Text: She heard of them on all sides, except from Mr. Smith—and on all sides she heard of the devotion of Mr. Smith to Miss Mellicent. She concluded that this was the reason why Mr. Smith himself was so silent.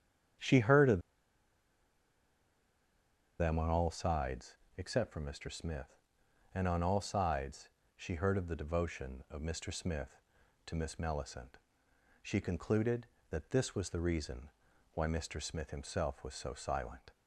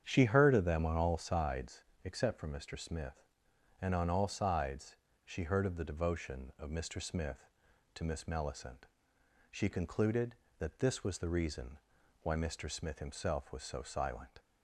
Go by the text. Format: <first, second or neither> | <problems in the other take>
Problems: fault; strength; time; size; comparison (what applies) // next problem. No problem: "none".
second | starts louder than the rest; strong; until 3.8 s; 8.5 dB; strong in the second // pauses between "of" and "them"; strong; at 0.9 s; 2.3 s long // pauses between "sides" and "she"; slight; at 7.6 s; 0.26 s long; slight in the second // pauses between "reason" and "why"; at 14.4 s; 0.44 s long; also in the second